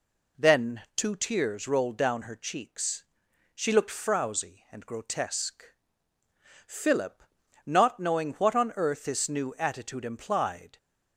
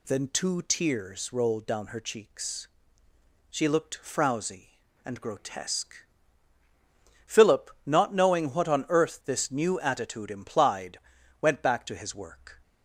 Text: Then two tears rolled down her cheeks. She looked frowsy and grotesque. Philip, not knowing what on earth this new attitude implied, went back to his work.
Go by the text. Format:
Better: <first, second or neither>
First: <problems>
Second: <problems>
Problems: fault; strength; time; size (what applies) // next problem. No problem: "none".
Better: second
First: pauses between "Then" and "two"; slight; at 0.8 s; 0.16 s long // stops before "went back to his work"; at 10.7 s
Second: none